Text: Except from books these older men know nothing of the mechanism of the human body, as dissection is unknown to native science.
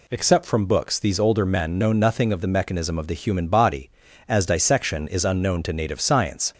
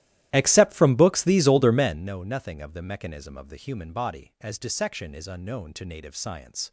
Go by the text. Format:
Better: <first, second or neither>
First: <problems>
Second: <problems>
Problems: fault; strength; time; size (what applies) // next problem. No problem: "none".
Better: first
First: none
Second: starts louder than the rest; strong; until 2.1 s; 14.5 dB